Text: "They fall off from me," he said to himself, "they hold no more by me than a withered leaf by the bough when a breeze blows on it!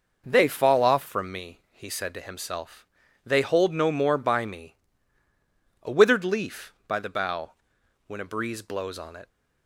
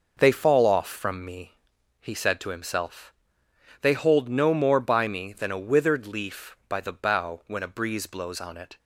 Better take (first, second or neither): second